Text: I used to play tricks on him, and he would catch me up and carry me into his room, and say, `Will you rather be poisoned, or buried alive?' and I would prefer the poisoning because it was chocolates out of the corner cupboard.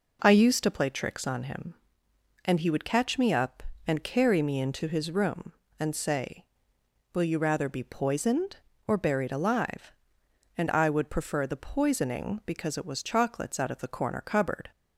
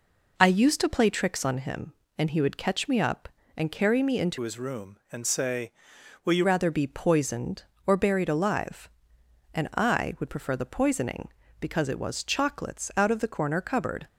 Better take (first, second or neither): first